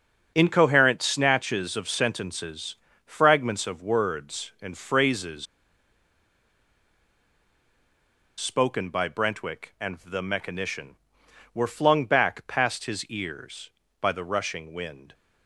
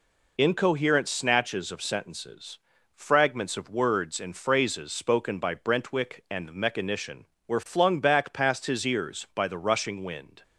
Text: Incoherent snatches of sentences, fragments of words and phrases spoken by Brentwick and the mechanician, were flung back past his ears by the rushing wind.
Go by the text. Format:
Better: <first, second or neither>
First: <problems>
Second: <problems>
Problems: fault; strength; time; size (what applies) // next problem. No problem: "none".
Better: second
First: starts louder than the rest; until 1.3 s; 6.5 dB // pauses between "phrases" and "spoken"; strong; at 5.4 s; 2.9 s long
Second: none